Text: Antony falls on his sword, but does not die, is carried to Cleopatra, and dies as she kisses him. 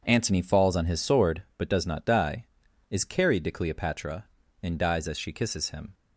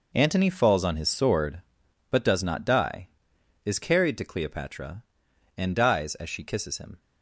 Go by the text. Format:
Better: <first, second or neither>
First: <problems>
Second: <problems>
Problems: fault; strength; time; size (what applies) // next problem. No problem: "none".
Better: first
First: none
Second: gets quieter; strong; throughout; 12 dB